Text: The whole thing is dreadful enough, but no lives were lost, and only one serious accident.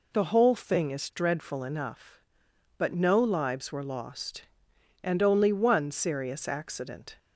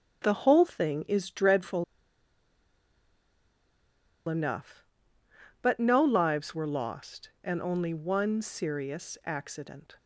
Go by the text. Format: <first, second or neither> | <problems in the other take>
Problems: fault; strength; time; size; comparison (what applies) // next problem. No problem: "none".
first | starts louder than the rest; strong; until 1.2 s; 9 dB // pauses between "dreadful" and "enough"; strong; at 1.8 s; 2.4 s long